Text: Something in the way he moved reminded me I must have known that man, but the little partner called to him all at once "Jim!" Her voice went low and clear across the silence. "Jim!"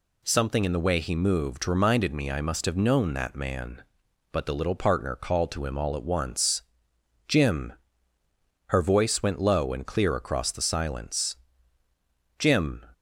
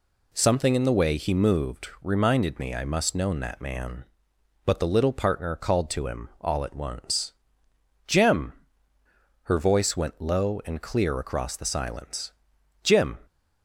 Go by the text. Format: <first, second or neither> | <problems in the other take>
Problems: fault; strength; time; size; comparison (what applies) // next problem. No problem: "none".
first | skips "have"; at 3.1 s // pauses between "once" and "Jim"; noticeable; at 7.3 s; 0.74 s long; noticeable in the first